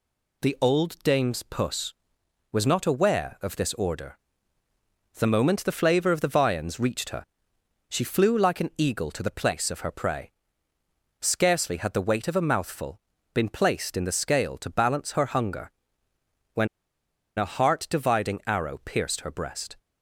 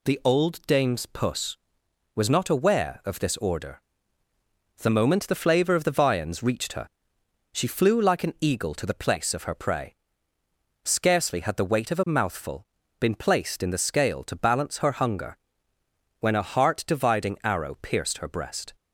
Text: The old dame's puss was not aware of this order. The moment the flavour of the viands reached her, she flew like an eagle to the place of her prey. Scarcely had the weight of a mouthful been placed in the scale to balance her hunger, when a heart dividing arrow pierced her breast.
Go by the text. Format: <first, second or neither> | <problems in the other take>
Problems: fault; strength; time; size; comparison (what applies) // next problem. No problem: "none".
second | pauses between "mouthful" and "been"; slight; at 12.9 s; 0.34 s long; slight in the second // pauses between "when" and "a"; noticeable; at 16.6 s; 0.70 s long